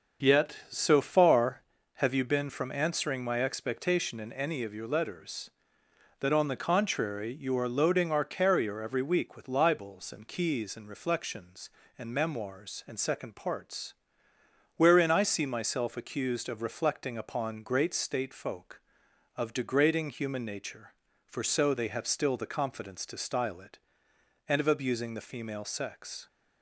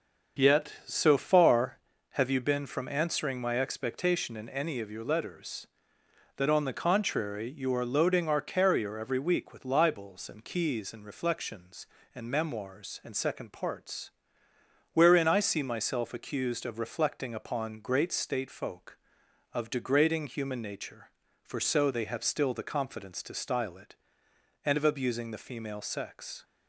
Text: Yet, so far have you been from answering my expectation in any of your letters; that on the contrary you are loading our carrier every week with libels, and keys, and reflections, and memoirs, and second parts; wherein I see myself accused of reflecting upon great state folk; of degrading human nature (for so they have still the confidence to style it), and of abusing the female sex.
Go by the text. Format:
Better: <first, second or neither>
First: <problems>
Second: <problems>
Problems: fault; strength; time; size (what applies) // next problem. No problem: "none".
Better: neither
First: starts louder than the rest; until 1.3 s; 6.5 dB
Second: starts louder than the rest; until 1.5 s; 6.5 dB